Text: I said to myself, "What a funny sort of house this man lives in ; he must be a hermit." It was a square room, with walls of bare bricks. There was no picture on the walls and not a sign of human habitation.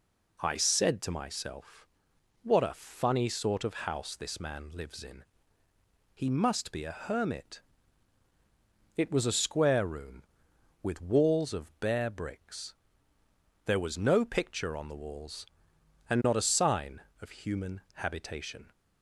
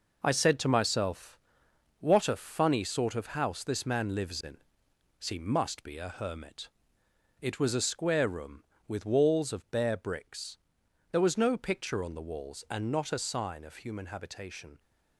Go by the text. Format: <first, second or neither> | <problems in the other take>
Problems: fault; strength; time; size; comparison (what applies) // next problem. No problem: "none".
first | gets quieter; strong; throughout; 8.5 dB